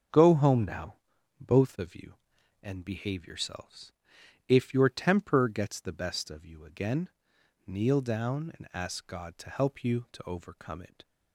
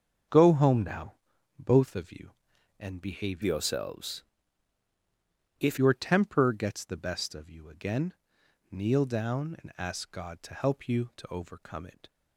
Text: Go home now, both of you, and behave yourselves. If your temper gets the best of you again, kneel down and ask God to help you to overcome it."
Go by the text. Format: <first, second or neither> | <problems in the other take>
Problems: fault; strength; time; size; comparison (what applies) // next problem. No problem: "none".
first | starts louder than the rest; until 1.7 s; 7 dB; strong in the first // changes voice from "yourselves" to "If"; from 3.4 to 5.7 s; 2.3 s long